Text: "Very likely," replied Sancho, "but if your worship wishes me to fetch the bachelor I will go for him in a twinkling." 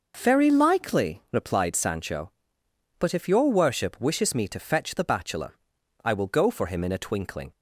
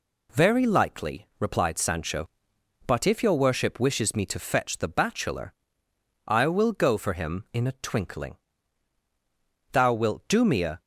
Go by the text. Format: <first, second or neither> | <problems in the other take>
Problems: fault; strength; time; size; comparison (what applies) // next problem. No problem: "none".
first | pauses between "bachelor" and "I"; noticeable; at 5.5 s; 0.74 s long; noticeable in the first // goes on to say "Thou wilt do me a"; noticeable; from 9.7 s on; 1.0 s long